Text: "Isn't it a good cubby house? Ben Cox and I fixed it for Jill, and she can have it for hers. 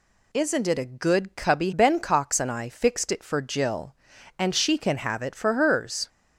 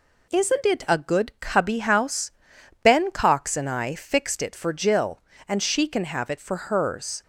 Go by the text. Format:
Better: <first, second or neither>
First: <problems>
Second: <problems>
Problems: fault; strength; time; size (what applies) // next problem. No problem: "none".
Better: second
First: skips "house"; at 1.7 s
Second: none